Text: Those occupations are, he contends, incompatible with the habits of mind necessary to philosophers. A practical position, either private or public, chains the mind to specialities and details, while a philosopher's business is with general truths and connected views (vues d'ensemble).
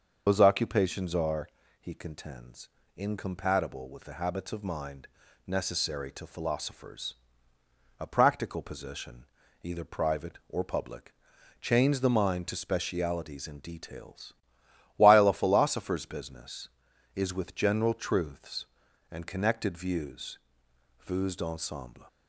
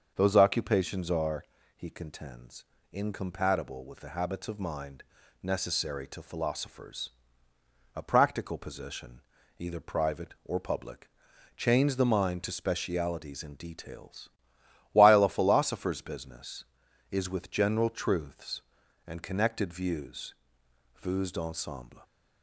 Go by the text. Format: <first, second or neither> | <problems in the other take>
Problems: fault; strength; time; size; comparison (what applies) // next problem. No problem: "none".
second | loses the start of "Those"; at 0.2 s; 75 ms // starts louder than the rest; until 1.2 s; 6 dB; also in the second // pauses between "mind" and "necessary"; at 5.0 s; 0.38 s long; also in the second